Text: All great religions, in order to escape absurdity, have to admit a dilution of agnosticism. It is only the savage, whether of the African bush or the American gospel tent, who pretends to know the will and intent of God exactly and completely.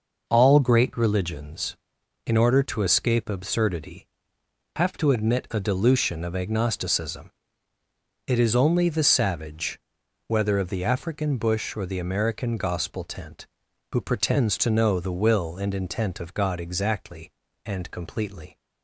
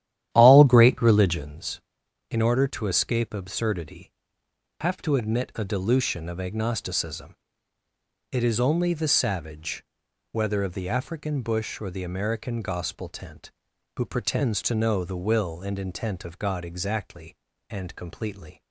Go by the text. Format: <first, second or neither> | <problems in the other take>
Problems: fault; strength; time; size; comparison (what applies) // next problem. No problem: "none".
first | starts louder than the rest; strong; until 1.5 s; 11.5 dB